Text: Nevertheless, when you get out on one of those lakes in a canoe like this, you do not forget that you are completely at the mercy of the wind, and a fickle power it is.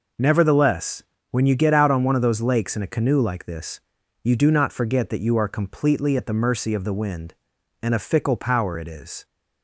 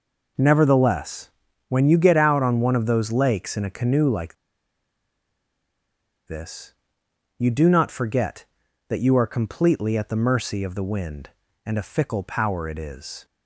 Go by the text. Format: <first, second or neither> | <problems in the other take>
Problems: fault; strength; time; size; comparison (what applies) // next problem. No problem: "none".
first | pauses between "like" and "this"; strong; at 4.3 s; 1.9 s long